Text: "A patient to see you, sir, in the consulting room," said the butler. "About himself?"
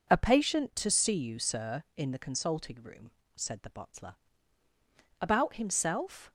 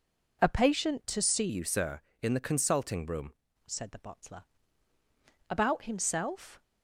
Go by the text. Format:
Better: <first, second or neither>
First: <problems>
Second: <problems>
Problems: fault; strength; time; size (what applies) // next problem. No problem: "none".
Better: first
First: none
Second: changes voice from "you" to "room"; from 1.4 to 3.3 s; 1.9 s long